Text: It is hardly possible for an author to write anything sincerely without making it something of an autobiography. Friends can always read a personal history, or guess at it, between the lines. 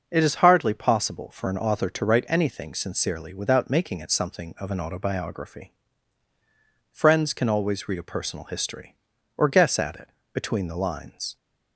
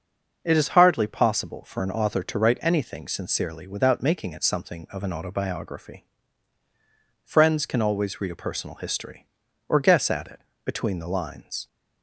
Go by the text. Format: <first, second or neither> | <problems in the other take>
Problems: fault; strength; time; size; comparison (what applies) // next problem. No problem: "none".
neither | starts louder than the rest; noticeable; the same in both